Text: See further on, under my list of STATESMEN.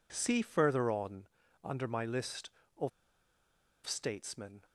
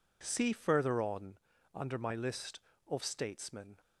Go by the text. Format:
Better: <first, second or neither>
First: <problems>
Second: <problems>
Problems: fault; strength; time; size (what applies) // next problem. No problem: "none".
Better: second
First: pauses between "of" and "STATESMEN"; noticeable; at 2.8 s; 0.96 s long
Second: none